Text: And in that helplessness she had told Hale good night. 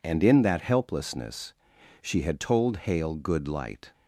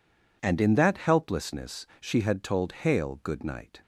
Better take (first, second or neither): second